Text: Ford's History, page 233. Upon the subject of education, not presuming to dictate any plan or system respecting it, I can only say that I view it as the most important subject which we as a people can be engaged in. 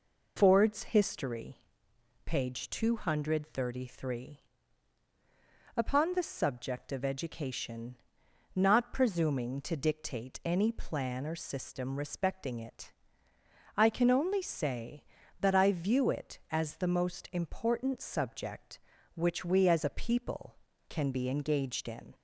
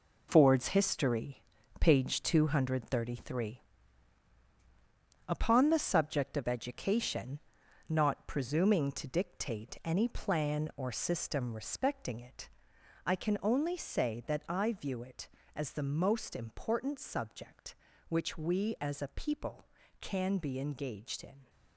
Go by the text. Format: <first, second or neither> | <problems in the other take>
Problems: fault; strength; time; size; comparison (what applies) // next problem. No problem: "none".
first | gets quieter; strong; throughout; 9 dB